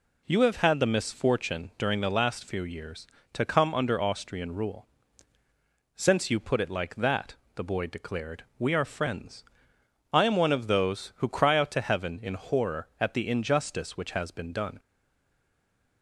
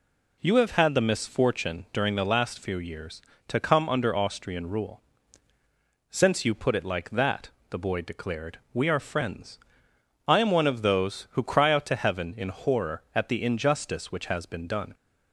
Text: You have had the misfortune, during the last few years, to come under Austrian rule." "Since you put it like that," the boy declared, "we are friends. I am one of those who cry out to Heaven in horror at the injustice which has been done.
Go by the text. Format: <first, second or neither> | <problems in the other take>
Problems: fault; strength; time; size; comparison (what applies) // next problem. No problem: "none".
second | stays silent after the last word; noticeable; from 14.7 s on; 1.3 s long